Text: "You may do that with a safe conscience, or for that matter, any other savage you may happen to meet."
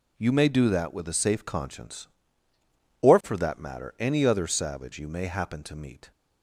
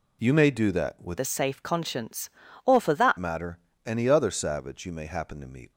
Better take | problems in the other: first | changes voice from "a" to "that"; from 1.1 to 3.1 s; 2.0 s long

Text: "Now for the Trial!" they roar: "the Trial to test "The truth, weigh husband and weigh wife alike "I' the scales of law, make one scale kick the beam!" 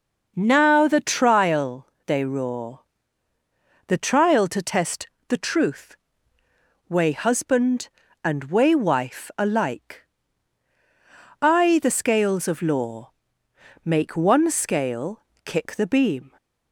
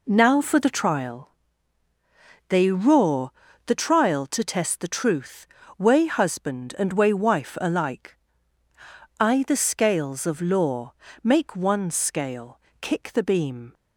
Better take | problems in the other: second | skips "for"; at 0.8 s // pauses between "test" and "The"; slight; at 5.0 s; 0.22 s long // pauses between "alike" and "I"; strong; at 10.0 s; 1.3 s long; also in the second // pauses between "scale" and "kick"; slight; at 15.2 s; 0.22 s long; slight in the second

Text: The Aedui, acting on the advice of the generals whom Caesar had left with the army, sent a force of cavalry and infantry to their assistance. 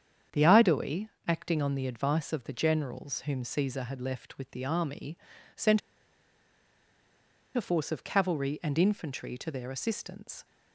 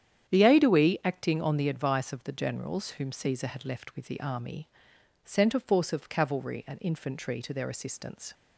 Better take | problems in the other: second | starts louder than the rest; strong; until 1.5 s; 8 dB; strong in the second // pauses between "sent" and "a"; strong; at 5.8 s; 1.7 s long

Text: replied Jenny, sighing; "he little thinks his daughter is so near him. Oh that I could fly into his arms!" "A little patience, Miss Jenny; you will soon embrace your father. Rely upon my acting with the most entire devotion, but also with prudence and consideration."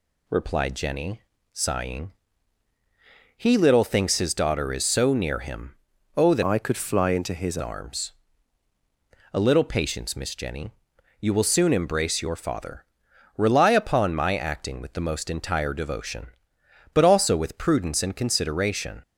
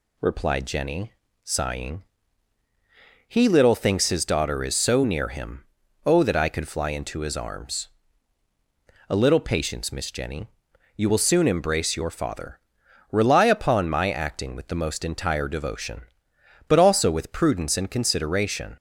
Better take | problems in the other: second | changes voice from "I" to "his"; from 6.4 to 7.5 s; 1.1 s long

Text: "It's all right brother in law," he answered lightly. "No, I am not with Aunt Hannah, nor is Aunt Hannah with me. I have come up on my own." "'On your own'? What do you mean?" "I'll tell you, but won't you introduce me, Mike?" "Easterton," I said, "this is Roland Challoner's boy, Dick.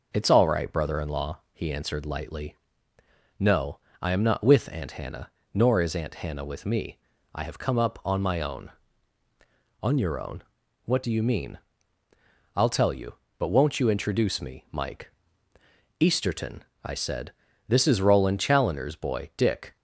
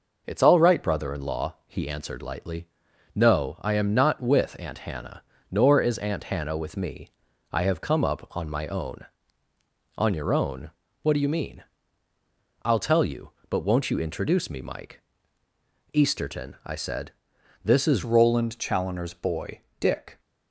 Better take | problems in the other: first | changes voice at "Roland"; from 18.0 s on; 2.1 s long

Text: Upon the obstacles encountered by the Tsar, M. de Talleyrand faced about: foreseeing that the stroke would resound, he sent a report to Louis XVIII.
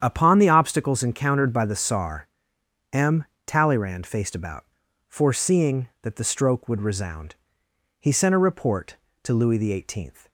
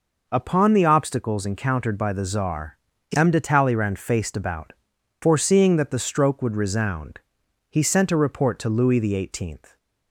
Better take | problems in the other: second | starts louder than the rest; strong; until 1.0 s; 9 dB // skips "de"; at 3.3 s

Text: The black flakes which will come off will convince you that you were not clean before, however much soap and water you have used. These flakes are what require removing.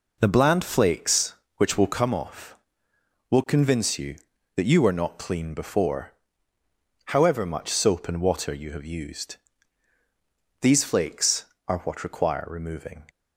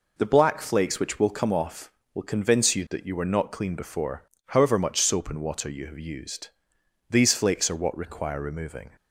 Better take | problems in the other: second | says "bland" for "black"; at 0.3 s

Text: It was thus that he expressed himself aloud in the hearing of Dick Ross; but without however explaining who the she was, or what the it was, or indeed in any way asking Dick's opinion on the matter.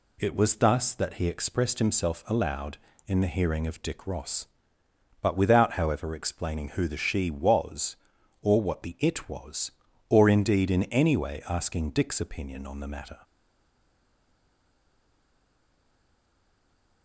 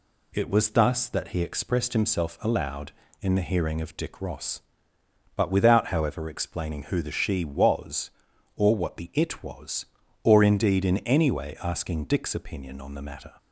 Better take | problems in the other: second | stays silent after the last word; strong; from 13.2 s on; 3.8 s long

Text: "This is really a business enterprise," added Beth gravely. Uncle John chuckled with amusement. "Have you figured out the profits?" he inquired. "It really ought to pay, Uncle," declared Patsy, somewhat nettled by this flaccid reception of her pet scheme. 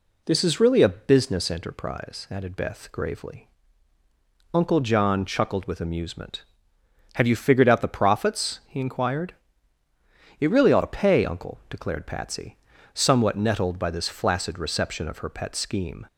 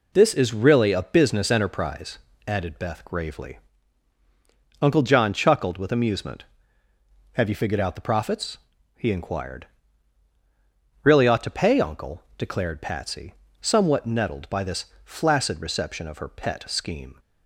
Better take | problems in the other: first | skips "It"; at 10.3 s // pauses between "this" and "flaccid"; slight; at 14.8 s; 0.18 s long

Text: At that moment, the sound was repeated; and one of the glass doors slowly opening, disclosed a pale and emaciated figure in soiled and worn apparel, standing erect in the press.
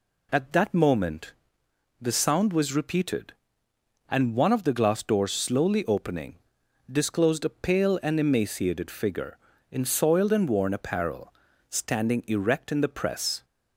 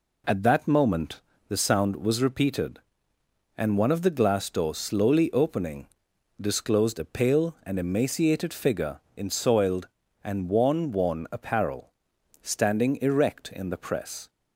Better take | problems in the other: first | says "worn" twice; at 10.9 s

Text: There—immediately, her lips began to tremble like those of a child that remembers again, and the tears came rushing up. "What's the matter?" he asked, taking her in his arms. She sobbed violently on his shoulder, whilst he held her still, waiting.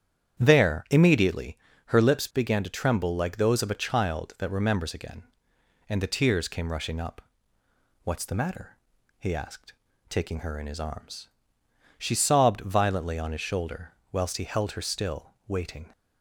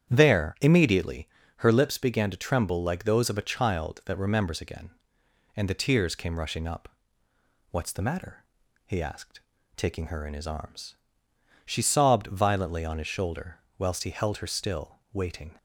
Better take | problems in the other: neither | starts louder than the rest; strong; the same in both

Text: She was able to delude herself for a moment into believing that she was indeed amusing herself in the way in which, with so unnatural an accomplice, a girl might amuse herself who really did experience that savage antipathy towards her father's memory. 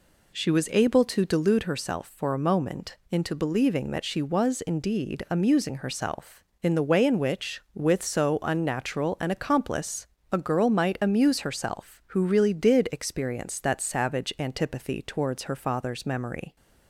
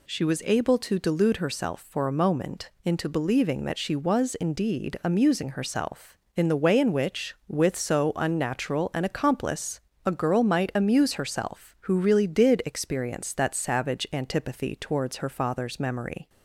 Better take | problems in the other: second | starts louder than the rest; slight; until 1.6 s; 3 dB // pauses between "moment" and "into"; slight; at 2.9 s; 0.16 s long; slight in the second

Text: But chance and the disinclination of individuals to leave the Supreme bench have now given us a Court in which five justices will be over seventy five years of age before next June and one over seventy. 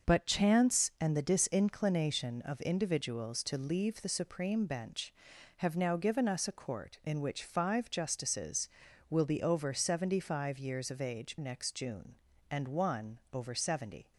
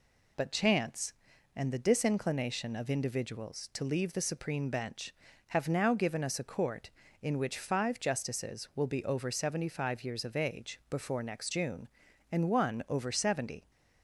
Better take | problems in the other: second | starts louder than the rest; until 1.1 s; 6.5 dB // skips "before"; at 11.3 s

